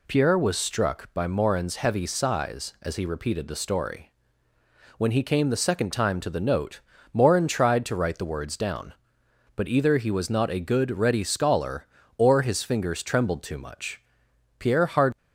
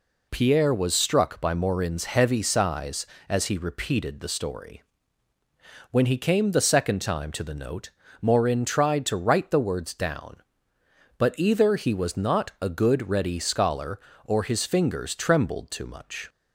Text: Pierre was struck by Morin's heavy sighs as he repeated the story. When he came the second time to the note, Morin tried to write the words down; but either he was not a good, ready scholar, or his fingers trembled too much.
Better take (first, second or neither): second